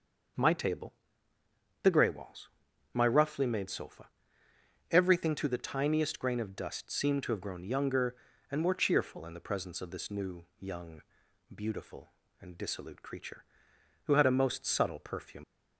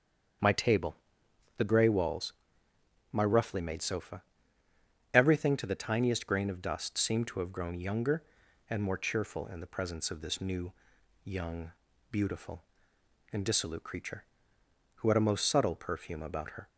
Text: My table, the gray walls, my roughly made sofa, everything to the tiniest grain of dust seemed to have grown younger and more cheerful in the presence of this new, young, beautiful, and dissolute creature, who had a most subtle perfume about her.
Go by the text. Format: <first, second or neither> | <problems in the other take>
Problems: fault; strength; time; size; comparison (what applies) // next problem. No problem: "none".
second | starts louder than the rest; noticeable; until 2.2 s; 6 dB; strong in the second // stops before "about her"; at 15.4 s